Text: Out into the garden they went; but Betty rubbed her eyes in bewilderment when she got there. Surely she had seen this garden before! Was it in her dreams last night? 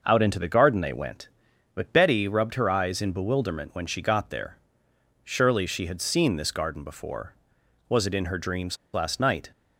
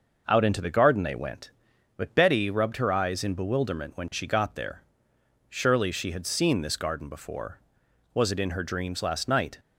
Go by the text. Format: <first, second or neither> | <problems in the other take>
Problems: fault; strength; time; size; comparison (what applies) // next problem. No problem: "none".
second | pauses between "dreams" and "last"; slight; at 8.7 s; 0.17 s long